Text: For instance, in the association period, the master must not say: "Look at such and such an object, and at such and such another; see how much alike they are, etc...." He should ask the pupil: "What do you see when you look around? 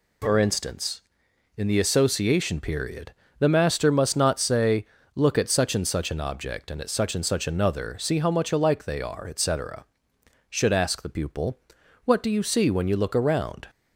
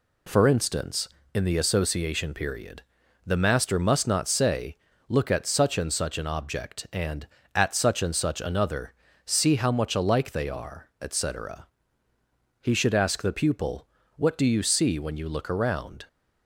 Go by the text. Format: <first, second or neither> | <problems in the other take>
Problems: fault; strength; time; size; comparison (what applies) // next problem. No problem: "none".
second | skips "He"; at 10.1 s